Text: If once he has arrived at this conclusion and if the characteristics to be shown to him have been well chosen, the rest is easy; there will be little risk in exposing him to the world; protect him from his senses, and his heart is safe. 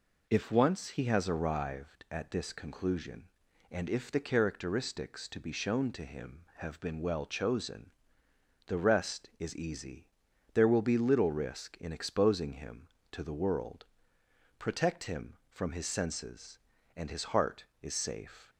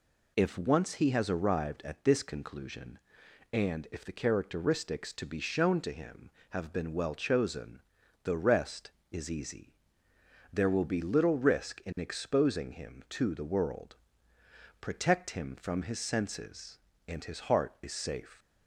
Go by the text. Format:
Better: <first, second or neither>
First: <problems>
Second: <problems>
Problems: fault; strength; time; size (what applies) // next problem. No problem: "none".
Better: neither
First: none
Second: none